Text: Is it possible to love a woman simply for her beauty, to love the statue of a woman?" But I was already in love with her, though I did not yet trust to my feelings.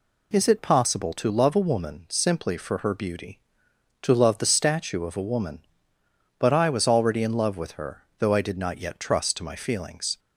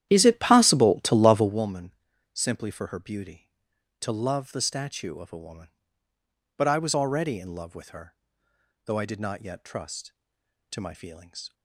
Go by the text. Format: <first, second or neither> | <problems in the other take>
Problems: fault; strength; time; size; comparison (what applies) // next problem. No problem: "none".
first | starts louder than the rest; strong; until 1.7 s; 11.5 dB // pauses between "woman" and "simply"; at 1.9 s; 0.40 s long